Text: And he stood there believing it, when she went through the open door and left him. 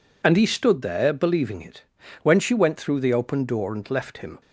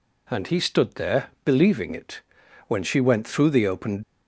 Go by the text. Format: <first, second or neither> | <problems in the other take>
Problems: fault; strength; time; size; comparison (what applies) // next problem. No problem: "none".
first | pauses between "there" and "believing"; slight; at 1.2 s; 0.18 s long // stops before "door and left him"; at 4.0 s